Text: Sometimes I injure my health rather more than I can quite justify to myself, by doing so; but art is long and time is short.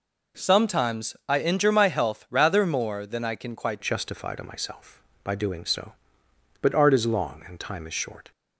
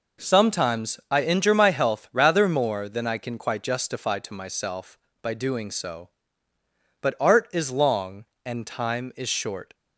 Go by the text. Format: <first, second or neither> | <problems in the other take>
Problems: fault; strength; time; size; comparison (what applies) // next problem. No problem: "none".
second | changes voice at "justify"; from 3.8 s on; 4.5 s long